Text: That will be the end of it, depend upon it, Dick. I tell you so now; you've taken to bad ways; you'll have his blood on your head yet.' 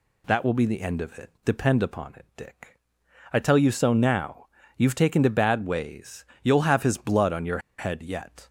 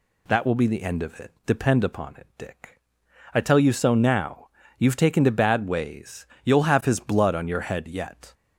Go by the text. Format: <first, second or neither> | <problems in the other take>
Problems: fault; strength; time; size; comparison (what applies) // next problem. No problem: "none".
second | pauses between "your" and "head"; slight; at 7.5 s; 0.19 s long